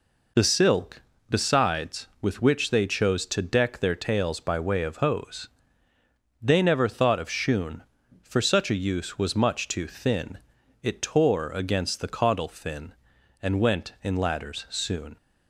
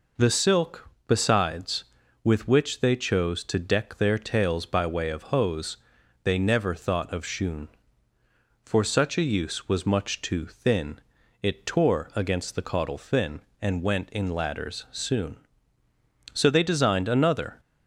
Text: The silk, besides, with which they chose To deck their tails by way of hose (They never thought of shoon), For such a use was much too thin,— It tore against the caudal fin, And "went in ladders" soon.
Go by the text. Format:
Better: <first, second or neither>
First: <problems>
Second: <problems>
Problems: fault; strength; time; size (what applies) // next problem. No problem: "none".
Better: first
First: none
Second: goes on to say "So they designed another"; noticeable; from 16.3 s on; 1.2 s long